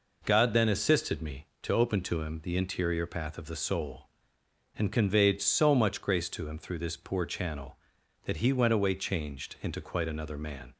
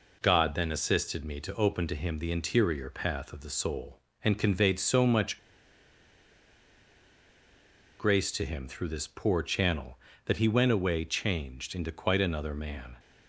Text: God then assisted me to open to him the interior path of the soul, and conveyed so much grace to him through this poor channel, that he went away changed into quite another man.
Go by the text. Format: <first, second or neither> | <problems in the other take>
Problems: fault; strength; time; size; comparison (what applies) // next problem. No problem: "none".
first | pauses between "much" and "grace"; strong; at 5.3 s; 2.6 s long